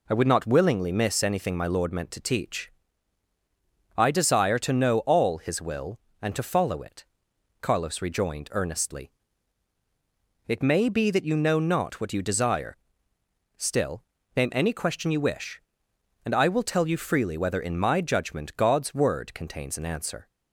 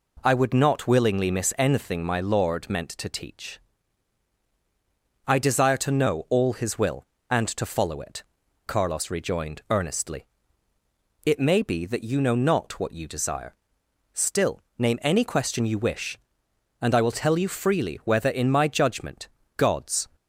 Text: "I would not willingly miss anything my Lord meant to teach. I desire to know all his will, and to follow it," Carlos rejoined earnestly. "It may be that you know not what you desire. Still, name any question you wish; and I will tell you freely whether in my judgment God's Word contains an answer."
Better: first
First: none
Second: pauses between "judgment" and "God's"; slight; at 19.2 s; 0.28 s long // stops before "Word contains an answer"; at 20.1 s

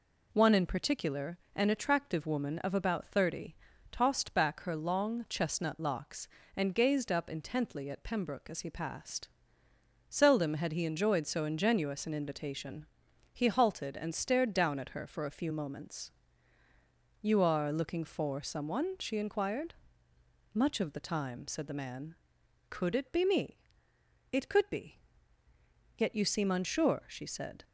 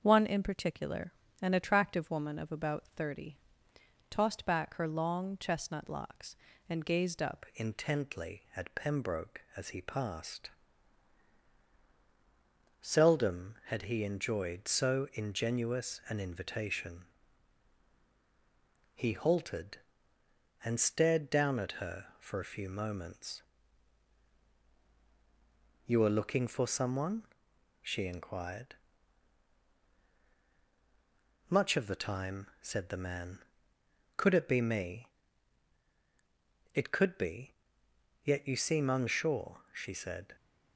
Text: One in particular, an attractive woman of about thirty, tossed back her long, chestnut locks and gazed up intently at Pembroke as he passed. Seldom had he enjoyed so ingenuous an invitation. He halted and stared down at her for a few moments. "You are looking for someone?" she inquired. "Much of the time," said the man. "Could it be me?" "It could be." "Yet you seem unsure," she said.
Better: first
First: none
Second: starts louder than the rest; until 1.0 s; 6.5 dB // changes voice at "intently"; from 7.5 s on; 32.8 s long

